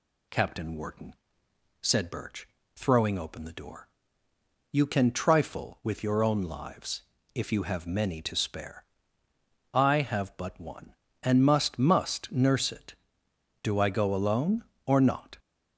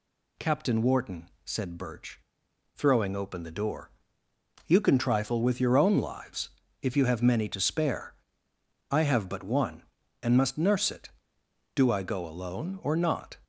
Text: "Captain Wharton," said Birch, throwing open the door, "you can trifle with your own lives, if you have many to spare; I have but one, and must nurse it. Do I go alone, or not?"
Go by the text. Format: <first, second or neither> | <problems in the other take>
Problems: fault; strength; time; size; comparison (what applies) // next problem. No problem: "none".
second | says "must" twice; at 11.7 s